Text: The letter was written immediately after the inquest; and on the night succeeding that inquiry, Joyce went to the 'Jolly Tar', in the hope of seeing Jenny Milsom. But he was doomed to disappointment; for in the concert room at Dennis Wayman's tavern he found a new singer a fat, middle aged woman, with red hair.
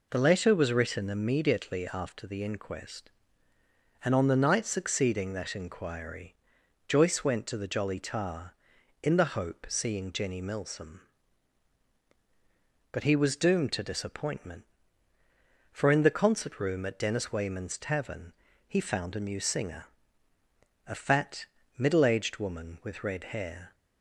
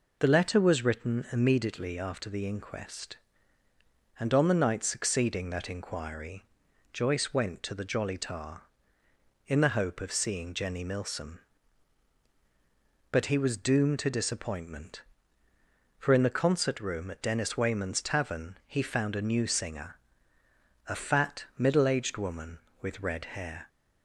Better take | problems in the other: second | skips "of"; at 9.6 s // pauses between "tavern" and "he"; slight; at 18.3 s; 0.34 s long // pauses between "singer" and "a"; at 19.8 s; 1.0 s long; noticeable in the second

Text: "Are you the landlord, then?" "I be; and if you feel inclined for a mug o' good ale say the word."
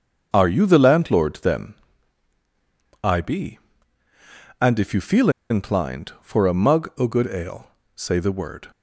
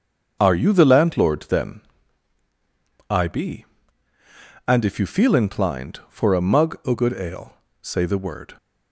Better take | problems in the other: second | starts louder than the rest; until 1.3 s; 7 dB; also in the second // pauses between "feel" and "inclined"; slight; at 5.2 s; 0.20 s long // pauses between "ale" and "say"; slight; at 7.6 s; 0.26 s long; slight in the second

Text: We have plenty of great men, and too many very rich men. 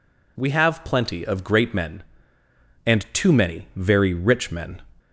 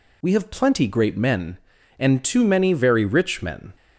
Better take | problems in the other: first | skips "of"; at 0.8 s

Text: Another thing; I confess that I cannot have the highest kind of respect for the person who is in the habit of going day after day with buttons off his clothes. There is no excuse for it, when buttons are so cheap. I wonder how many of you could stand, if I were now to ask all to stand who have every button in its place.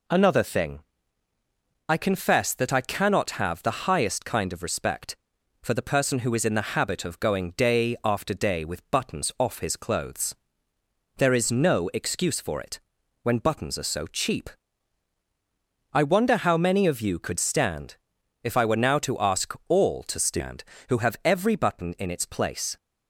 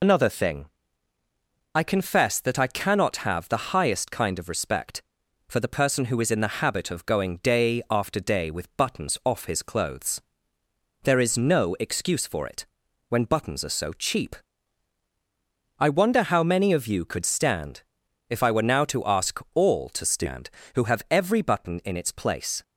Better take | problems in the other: first | loses the start of "Another"; at 0.0 s; 80 ms

